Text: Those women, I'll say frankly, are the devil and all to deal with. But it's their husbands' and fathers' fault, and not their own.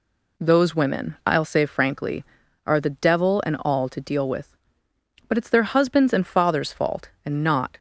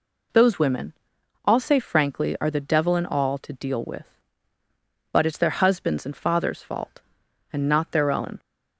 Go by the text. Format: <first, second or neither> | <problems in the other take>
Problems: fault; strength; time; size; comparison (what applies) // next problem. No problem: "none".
second | stops before "their own"; at 7.7 s